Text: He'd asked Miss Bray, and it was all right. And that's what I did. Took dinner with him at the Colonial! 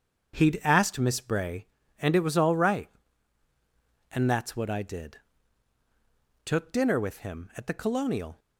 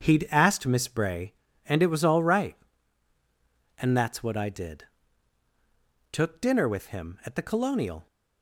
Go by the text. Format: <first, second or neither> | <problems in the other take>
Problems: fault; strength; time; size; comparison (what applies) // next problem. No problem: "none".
neither | starts louder than the rest; strong; the same in both